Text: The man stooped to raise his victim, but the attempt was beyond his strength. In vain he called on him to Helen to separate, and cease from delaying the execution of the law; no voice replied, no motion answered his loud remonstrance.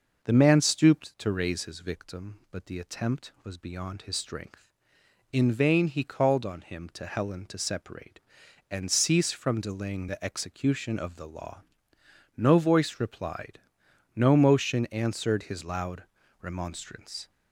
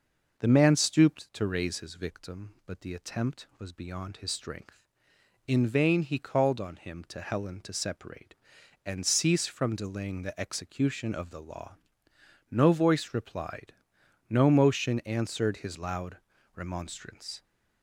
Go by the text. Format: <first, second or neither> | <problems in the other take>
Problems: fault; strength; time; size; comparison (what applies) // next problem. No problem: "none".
neither | pauses between "loud" and "remonstrance"; the same in both